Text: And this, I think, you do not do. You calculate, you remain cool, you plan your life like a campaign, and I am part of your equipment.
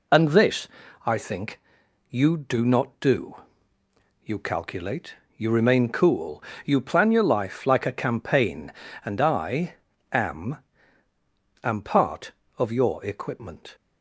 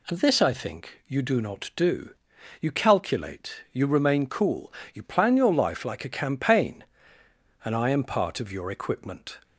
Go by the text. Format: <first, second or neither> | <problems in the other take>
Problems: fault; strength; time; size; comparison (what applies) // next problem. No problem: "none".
second | pauses between "I" and "am"; slight; at 9.7 s; 0.36 s long // says "am" twice; at 11.6 s